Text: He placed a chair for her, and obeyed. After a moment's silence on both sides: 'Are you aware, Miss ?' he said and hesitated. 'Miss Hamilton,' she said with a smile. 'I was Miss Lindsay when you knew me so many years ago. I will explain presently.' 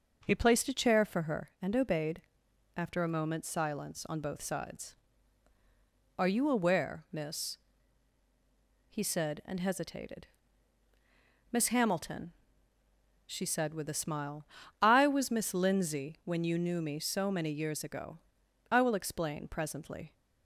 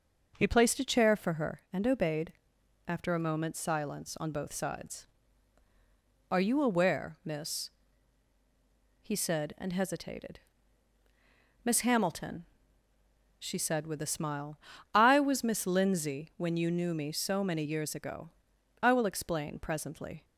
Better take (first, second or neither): neither